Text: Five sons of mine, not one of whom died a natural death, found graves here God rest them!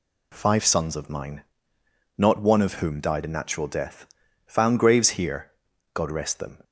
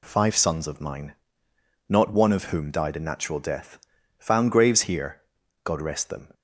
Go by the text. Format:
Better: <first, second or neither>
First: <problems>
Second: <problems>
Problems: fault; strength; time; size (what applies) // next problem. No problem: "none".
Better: neither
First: pauses between "here" and "God"; at 5.5 s; 0.42 s long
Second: pauses between "here" and "God"; at 5.2 s; 0.42 s long